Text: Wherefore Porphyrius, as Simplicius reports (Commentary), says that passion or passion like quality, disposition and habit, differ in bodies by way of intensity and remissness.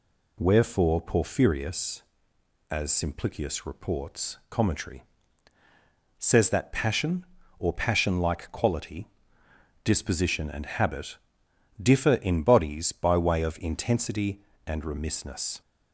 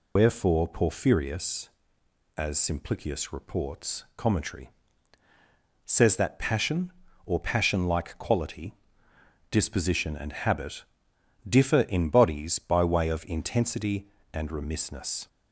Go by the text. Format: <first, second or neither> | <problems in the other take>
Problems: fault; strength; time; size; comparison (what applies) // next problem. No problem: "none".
first | loses the start of "Wherefore"; at 0.1 s; 110 ms